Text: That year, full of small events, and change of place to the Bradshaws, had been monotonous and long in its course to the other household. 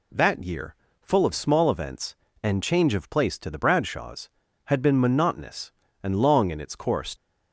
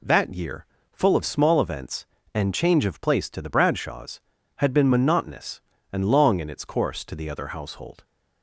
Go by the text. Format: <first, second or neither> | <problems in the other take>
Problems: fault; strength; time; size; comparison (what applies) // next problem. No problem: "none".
second | stops before "to the other household"; at 7.1 s